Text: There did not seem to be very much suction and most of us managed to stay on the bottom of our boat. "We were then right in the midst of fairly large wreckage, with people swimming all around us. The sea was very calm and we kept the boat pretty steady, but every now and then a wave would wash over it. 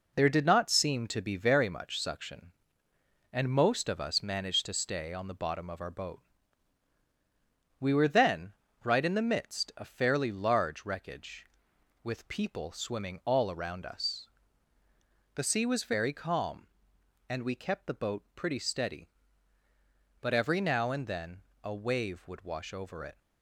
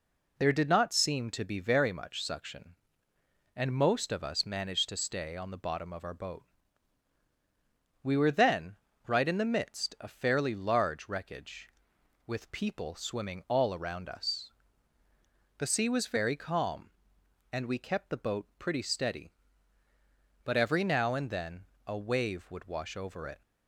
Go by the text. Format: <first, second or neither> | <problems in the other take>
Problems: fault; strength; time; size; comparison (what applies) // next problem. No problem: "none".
second | gets quieter; noticeable; throughout; 5.5 dB // pauses between "then" and "right"; slight; at 8.5 s; 0.32 s long; slight in the second // pauses between "then" and "a"; slight; at 21.4 s; 0.22 s long; slight in the second